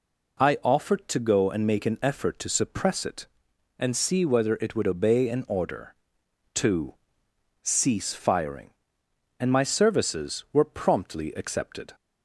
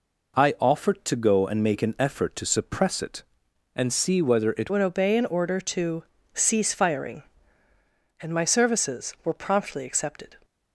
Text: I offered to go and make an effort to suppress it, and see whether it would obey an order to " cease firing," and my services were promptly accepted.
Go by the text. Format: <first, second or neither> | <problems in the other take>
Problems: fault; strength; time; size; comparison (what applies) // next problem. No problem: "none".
first | changes voice at "would"; from 4.7 s on; 5.6 s long